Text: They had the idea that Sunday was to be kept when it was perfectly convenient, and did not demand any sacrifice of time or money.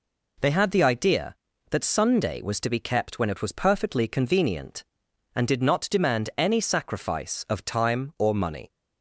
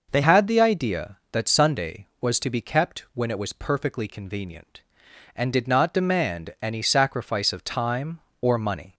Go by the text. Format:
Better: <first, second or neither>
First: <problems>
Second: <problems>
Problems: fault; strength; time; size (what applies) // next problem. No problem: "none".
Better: first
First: none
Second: changes voice at "had"; from 0.2 s on; 8.7 s long